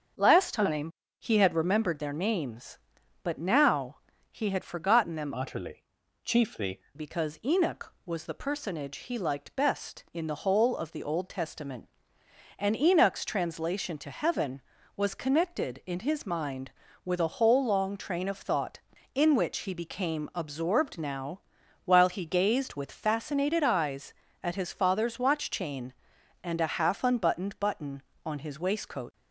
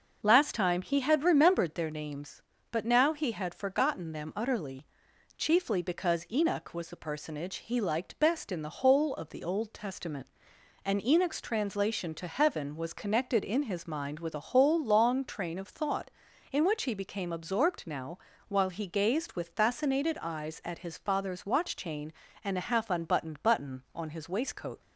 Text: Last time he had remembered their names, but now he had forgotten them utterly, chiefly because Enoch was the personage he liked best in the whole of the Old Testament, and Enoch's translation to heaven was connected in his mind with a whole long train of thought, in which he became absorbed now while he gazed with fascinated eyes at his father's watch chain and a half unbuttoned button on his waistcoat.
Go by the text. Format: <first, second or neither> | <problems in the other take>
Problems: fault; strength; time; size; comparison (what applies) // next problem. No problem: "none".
second | starts louder than the rest; until 1.4 s; 7 dB // pauses between "time" and "he"; slight; at 0.9 s; 0.28 s long // pauses between "now" and "he"; slight; at 3.9 s; 0.34 s long // changes voice from "utterly" to "chiefly"; from 5.3 to 6.8 s; 1.5 s long // pauses between "now" and "while"; noticeable; at 21.4 s; 0.46 s long; slight in the second